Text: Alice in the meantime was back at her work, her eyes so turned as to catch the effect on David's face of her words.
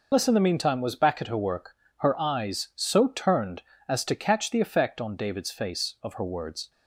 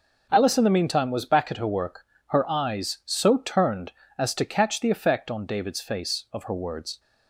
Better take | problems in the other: second | loses the start of "Alice"; at 0.1 s; 120 ms

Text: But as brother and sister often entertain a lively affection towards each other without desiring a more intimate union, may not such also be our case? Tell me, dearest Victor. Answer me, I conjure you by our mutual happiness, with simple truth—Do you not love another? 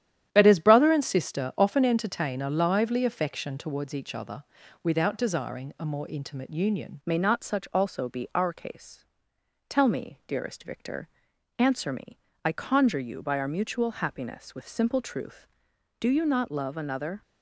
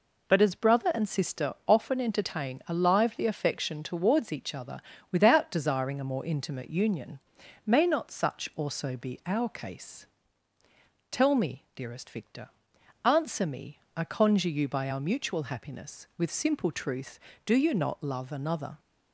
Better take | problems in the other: second | starts louder than the rest; strong; until 1.3 s; 10.5 dB // pauses between "other" and "without"; at 4.4 s; 0.40 s long; slight in the second // changes voice at "may"; from 7.0 s on; 10.2 s long

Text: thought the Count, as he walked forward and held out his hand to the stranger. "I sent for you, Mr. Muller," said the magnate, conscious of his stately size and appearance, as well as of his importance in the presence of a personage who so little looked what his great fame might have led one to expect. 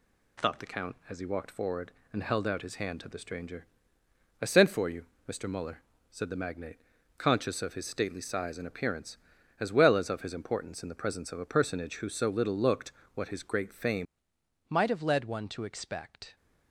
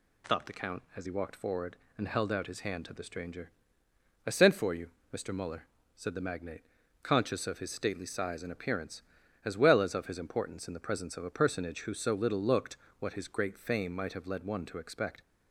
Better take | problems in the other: second | pauses between "looked" and "what"; slight; at 12.9 s; 0.22 s long; slight in the second // changes voice at "might"; from 14.6 s on; 1.7 s long

